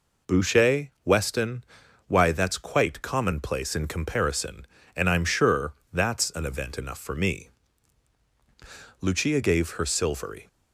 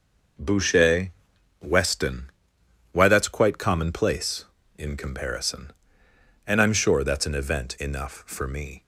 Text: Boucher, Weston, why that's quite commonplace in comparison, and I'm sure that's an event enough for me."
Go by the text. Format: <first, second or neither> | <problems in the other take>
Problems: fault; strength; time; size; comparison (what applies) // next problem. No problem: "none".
second | pauses between "sure" and "that's"; slight; at 5.7 s; 0.20 s long // goes on to say "Lucia gave her silvery"; from 9.0 s on; 1.4 s long